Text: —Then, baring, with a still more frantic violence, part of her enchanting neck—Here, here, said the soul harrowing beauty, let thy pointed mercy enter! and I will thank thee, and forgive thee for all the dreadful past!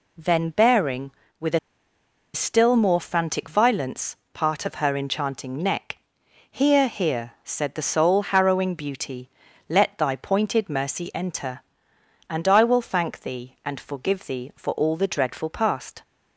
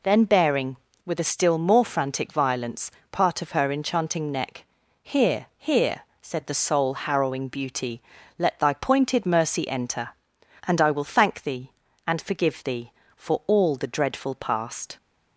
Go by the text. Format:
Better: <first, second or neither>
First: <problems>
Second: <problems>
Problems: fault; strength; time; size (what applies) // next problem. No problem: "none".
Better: second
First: pauses between "a" and "still"; noticeable; at 1.5 s; 0.75 s long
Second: none